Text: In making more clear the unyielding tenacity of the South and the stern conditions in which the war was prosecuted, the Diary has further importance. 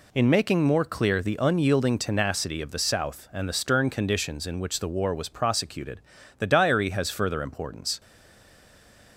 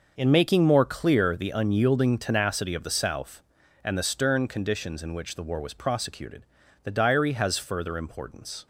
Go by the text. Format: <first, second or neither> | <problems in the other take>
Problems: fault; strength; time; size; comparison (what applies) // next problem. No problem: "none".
second | stays silent after the last word; noticeable; from 7.9 s on; 1.2 s long